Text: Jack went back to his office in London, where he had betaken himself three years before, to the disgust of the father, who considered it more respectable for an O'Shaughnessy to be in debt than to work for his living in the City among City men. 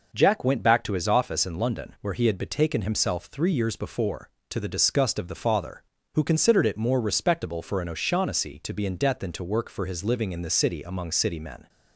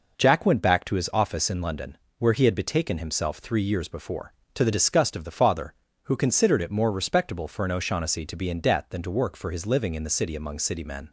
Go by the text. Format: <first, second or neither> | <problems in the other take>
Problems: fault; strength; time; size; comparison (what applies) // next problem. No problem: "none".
neither | none